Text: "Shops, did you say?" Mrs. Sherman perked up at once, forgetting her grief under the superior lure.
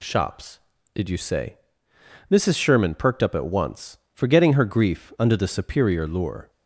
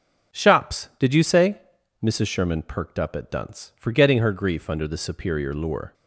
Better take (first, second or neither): first